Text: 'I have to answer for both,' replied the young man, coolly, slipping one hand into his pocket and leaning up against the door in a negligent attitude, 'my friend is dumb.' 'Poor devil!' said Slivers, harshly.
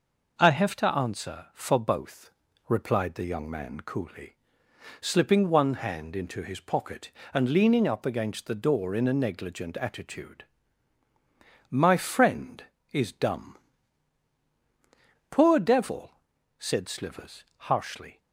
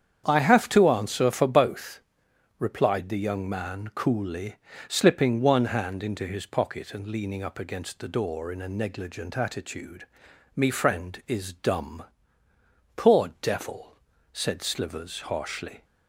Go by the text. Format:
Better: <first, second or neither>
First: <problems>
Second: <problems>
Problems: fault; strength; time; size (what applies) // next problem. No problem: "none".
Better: first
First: none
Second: starts louder than the rest; strong; until 1.2 s; 8.5 dB // says "me" for "my"; at 10.5 s